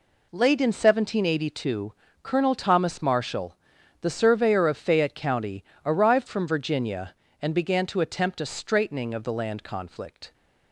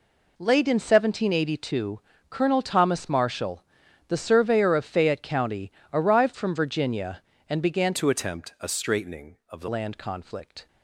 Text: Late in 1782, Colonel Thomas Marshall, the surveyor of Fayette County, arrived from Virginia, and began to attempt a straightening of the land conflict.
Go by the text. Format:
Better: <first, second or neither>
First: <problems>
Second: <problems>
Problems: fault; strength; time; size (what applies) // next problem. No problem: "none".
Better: first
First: none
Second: changes voice from "to" to "the"; from 7.9 to 9.6 s; 1.7 s long